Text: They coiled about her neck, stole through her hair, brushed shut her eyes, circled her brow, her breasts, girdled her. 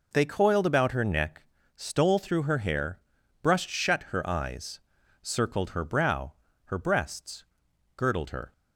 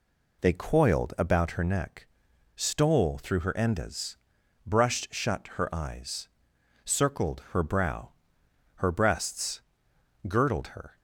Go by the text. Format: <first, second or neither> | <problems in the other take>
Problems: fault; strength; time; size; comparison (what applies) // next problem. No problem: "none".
first | says "endas" for "hair"; at 3.5 s